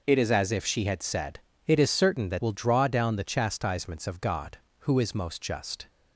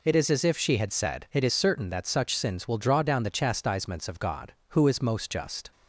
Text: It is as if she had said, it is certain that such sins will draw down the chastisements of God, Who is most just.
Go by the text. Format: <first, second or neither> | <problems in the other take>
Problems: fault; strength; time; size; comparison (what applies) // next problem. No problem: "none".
second | skips "such sins"; at 2.4 s